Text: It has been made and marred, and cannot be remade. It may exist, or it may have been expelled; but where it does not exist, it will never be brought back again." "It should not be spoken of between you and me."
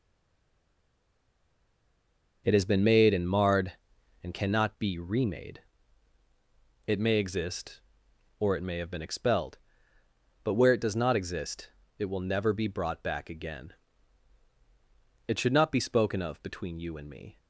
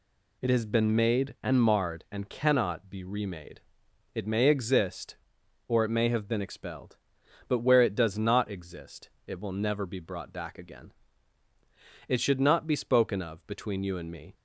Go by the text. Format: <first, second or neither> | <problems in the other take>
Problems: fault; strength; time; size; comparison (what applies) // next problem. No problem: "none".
second | stays silent before the first word; until 2.4 s; 2.4 s long